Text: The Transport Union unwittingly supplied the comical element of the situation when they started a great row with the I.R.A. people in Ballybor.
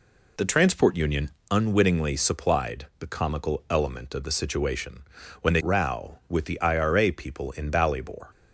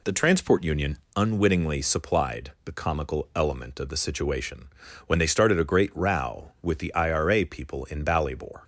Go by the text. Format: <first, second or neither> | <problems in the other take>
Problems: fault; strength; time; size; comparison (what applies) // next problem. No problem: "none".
second | pauses between "Union" and "unwittingly"; slight; at 1.3 s; 0.20 s long; slight in the second // pauses between "situation" and "when"; at 5.0 s; 0.40 s long; also in the second // skips "started a great"; at 5.6 s